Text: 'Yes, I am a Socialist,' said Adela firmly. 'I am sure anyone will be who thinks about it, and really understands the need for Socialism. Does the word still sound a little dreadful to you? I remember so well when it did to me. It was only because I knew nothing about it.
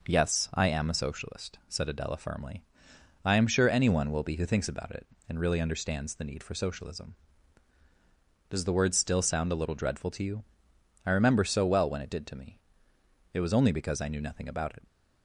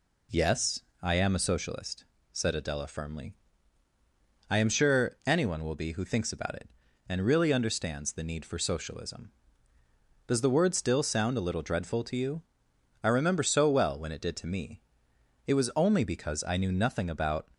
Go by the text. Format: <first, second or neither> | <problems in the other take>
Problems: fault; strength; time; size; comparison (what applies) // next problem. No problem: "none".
first | stops before "it"; at 17.5 s